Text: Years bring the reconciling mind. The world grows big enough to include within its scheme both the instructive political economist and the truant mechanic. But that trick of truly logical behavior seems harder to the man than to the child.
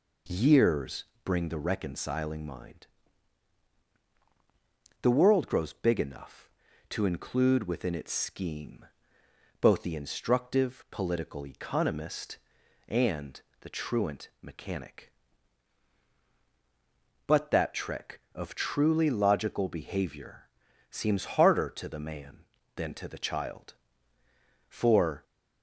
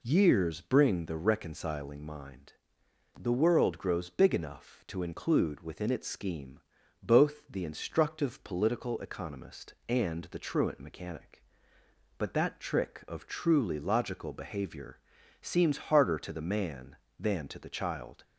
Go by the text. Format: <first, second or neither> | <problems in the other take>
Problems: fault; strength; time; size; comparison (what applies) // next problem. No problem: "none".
second | pauses between "Years" and "bring"; slight; at 1.0 s; 0.18 s long // pauses between "scheme" and "both"; noticeable; at 8.8 s; 0.76 s long; also in the second // pauses between "and" and "the"; slight; at 13.3 s; 0.22 s long // pauses between "behavior" and "seems"; at 20.4 s; 0.42 s long; noticeable in the second // goes on to say "For"; from 24.6 s on; 0.56 s long